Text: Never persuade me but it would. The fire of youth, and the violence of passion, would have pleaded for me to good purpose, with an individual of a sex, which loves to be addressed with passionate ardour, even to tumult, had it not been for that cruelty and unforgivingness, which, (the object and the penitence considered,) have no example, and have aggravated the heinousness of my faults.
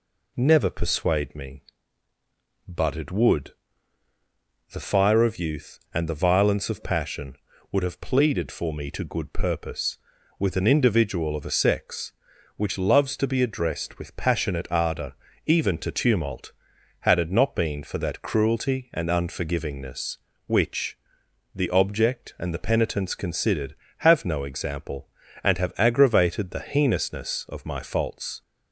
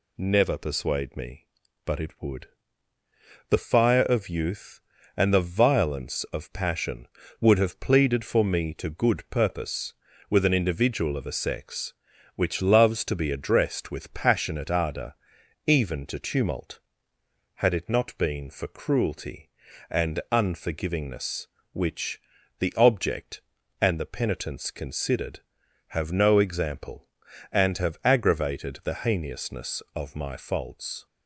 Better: first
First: none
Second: skips "that"; at 18.6 s

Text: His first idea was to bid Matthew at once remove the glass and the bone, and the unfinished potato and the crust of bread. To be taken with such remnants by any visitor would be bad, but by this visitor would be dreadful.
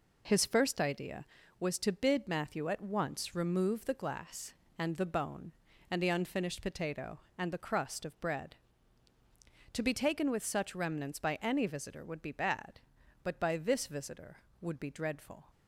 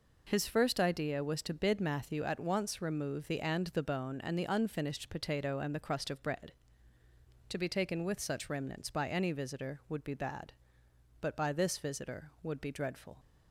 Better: first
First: none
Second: skips "glass"; at 3.3 s

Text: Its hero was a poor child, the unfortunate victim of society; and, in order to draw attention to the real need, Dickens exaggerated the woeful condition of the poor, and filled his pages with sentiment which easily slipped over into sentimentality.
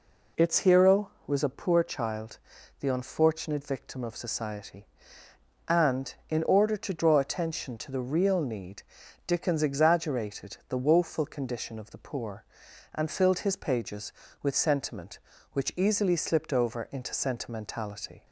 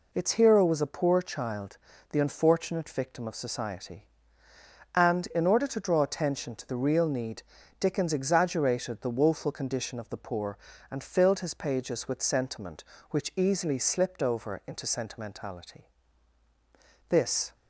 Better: first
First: none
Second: goes on to say "This"; slight; from 17.0 s on; 0.46 s long

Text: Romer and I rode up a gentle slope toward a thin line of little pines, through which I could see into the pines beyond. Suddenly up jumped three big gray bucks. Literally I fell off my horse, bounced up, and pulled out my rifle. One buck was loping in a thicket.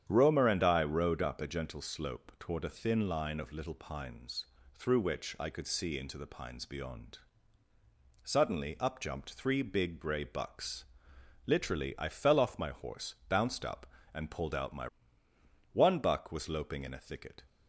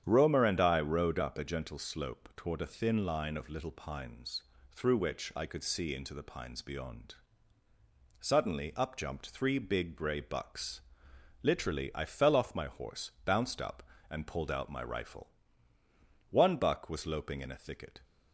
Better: second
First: starts louder than the rest; strong; until 1.0 s; 9 dB // skips "rifle"; at 15.3 s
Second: starts louder than the rest; strong; until 1.0 s; 9 dB

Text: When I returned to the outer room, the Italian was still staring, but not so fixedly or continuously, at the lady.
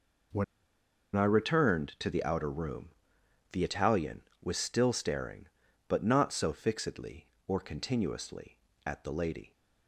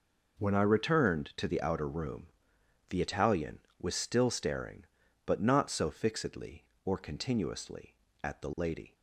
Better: second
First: pauses between "When" and "I"; noticeable; at 0.4 s; 0.70 s long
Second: none

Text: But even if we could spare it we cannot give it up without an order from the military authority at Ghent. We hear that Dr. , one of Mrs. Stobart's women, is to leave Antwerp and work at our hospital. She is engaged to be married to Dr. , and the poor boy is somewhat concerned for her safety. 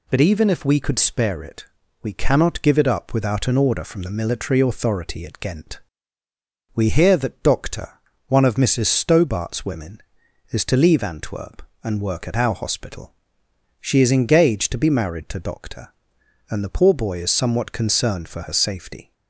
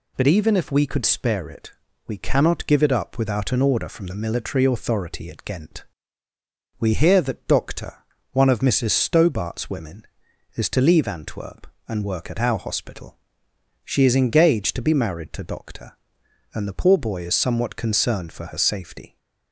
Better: neither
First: pauses between "it" and "we"; at 1.6 s; 0.38 s long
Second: pauses between "it" and "we"; slight; at 1.7 s; 0.36 s long

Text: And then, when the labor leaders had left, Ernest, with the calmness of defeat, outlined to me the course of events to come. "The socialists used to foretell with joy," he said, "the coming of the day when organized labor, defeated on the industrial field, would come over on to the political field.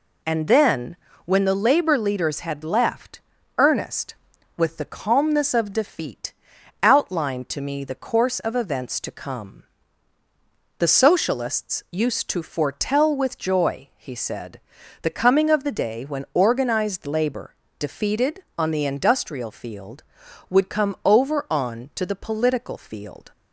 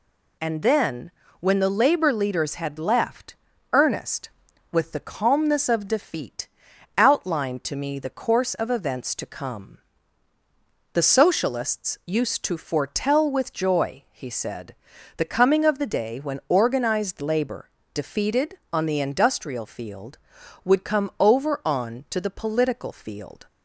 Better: second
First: starts louder than the rest; slight; until 1.4 s; 3.5 dB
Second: none

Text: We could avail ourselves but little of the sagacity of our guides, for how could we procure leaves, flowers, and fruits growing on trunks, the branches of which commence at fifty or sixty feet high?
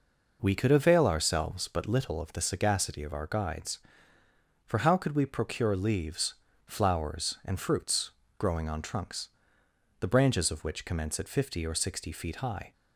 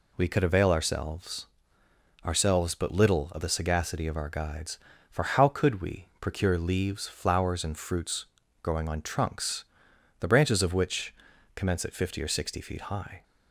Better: first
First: pauses between "fruits" and "growing"; slight; at 8.1 s; 0.26 s long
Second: says "ourselves" twice; at 2.2 s // pauses between "fruits" and "growing"; slight; at 8.2 s; 0.34 s long // pauses between "which" and "commence"; at 11.1 s; 0.42 s long

